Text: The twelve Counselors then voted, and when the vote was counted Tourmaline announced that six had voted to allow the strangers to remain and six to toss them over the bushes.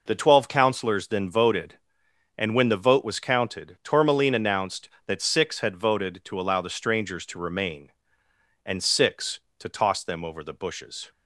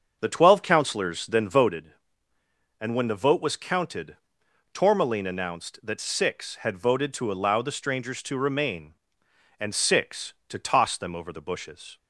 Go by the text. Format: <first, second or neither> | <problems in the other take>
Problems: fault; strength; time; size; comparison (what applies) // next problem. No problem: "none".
first | starts louder than the rest; until 1.9 s; 7 dB // pauses between "counted" and "Tourmaline"; noticeable; at 4.1 s; 0.56 s long